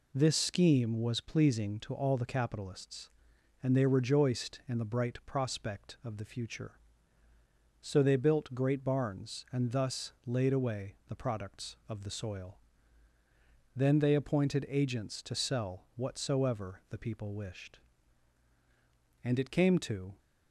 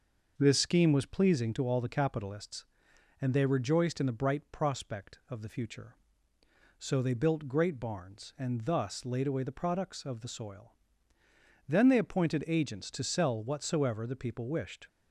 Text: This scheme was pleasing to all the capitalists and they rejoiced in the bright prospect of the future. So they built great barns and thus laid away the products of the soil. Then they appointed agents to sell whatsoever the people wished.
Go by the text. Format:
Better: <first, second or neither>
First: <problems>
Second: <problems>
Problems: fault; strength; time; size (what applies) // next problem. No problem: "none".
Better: second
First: goes on to say "And it came to"; noticeable; from 19.2 s on; 0.94 s long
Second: none